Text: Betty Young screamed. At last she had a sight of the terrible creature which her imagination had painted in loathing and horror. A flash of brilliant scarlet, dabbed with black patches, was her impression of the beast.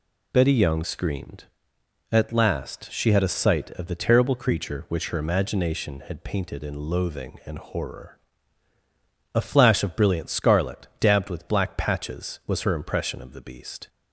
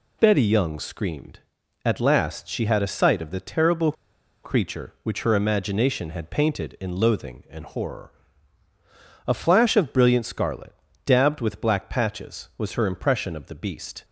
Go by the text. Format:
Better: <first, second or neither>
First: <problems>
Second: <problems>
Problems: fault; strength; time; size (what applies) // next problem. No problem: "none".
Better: first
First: none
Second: pauses between "terrible" and "creature"; noticeable; at 3.9 s; 0.51 s long